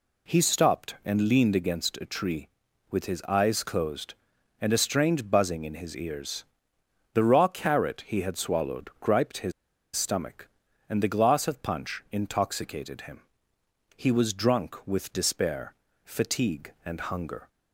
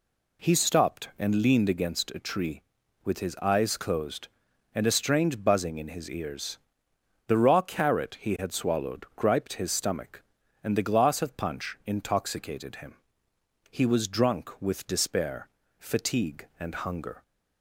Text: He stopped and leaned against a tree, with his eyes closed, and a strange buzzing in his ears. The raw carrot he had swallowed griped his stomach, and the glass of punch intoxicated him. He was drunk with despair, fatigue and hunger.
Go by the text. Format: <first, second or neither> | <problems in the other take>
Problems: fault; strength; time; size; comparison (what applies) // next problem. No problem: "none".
second | pauses between "his" and "stomach"; at 9.5 s; 0.43 s long